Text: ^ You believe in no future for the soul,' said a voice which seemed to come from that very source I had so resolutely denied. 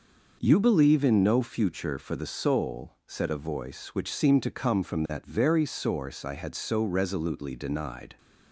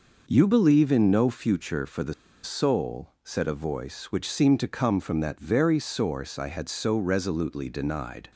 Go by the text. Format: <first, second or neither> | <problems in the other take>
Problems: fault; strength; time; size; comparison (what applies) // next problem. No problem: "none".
first | pauses between "the" and "soul"; slight; at 2.1 s; 0.30 s long